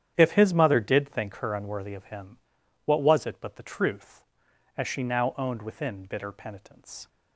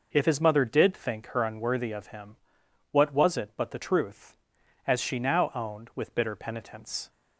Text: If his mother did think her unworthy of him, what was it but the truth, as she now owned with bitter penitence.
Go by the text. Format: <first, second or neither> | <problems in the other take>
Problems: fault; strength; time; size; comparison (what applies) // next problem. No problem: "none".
second | starts louder than the rest; strong; until 1.1 s; 9.5 dB // says "within" for "with"; at 5.6 s